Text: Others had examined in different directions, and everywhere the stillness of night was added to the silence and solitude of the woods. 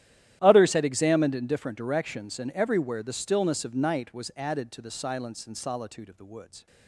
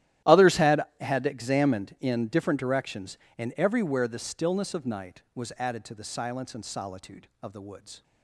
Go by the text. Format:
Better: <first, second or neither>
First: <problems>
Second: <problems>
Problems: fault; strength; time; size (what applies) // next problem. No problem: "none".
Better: first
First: starts louder than the rest; strong; until 1.4 s; 12.5 dB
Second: starts louder than the rest; strong; until 1.4 s; 13 dB // says "had" twice; at 1.0 s